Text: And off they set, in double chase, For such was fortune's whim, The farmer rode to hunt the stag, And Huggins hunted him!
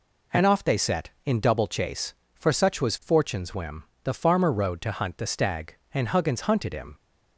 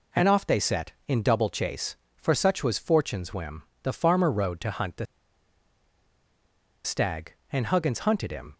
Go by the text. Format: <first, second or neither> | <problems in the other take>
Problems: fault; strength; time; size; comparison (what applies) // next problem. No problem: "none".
first | pauses between "the" and "stag"; strong; at 5.0 s; 1.8 s long